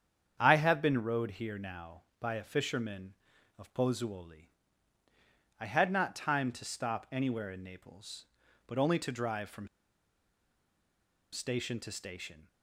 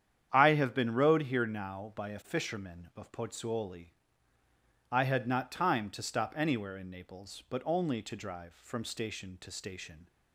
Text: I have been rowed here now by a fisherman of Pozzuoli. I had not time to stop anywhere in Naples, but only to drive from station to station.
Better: second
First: starts louder than the rest; strong; until 1.4 s; 8 dB // pauses between "from" and "station"; strong; at 9.6 s; 1.6 s long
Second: starts louder than the rest; strong; until 1.3 s; 9 dB

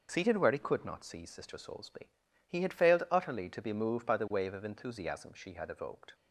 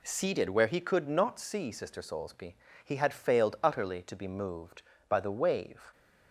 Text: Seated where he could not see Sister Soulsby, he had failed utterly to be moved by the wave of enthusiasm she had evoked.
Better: first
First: none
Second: stops before "of enthusiasm she had evoked"; at 5.9 s

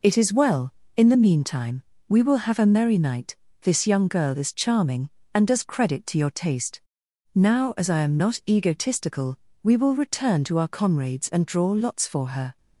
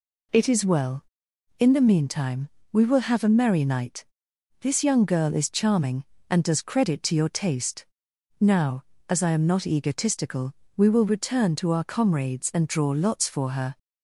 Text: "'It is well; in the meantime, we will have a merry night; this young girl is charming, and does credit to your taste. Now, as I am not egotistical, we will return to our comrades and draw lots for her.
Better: neither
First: none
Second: none

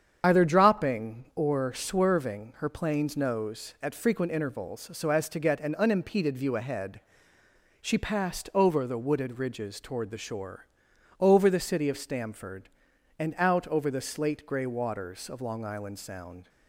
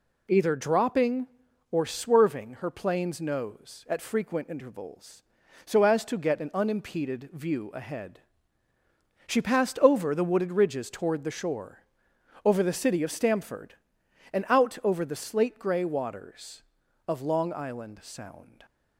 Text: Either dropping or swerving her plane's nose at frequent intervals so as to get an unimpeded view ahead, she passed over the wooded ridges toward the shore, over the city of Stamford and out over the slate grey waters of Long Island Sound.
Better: second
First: loses the start of "Either"; at 0.2 s; 55 ms // starts louder than the rest; strong; until 1.2 s; 8 dB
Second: none

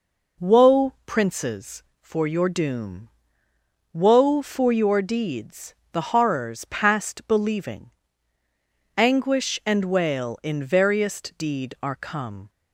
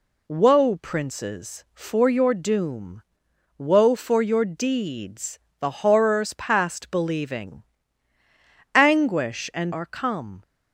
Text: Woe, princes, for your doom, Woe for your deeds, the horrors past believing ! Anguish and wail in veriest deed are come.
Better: first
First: none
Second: skips "wail in veriest deed"; at 9.7 s

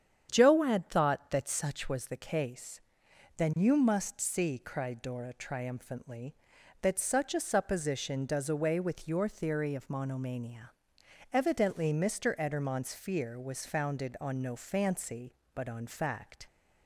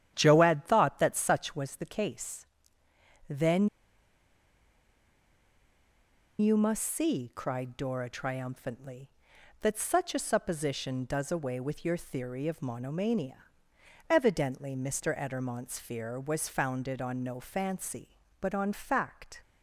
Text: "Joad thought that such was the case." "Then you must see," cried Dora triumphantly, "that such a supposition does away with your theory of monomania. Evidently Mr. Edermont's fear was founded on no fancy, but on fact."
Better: first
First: starts louder than the rest; strong; until 1.3 s; 9 dB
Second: starts louder than the rest; strong; until 1.1 s; 10.5 dB // pauses between "Then" and "you"; strong; at 3.6 s; 2.7 s long

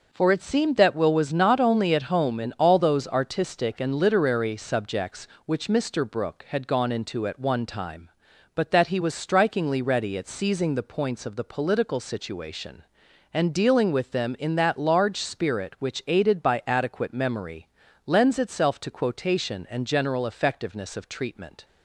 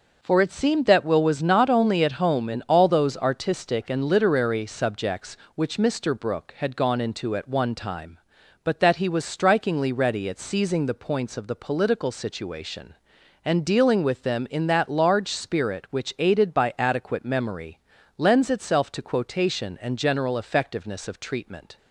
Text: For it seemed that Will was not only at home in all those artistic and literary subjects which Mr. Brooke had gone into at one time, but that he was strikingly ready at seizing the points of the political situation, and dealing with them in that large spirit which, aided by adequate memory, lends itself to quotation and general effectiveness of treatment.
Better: neither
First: none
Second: none

